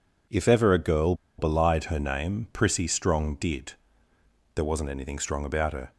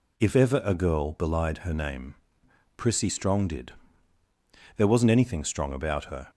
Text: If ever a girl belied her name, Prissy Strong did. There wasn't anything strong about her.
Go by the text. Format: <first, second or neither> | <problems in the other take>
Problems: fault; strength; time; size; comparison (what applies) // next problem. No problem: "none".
second | pauses between "girl" and "belied"; slight; at 1.1 s; 0.24 s long